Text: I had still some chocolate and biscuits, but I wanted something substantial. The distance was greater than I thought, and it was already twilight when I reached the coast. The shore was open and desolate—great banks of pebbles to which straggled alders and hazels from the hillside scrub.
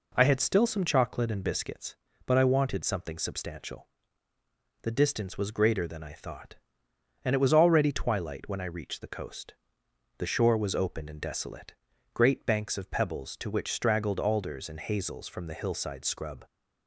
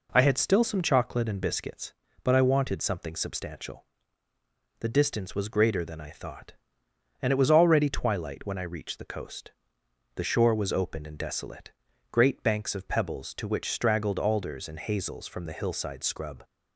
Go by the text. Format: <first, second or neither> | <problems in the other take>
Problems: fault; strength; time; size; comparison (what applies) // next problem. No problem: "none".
neither | none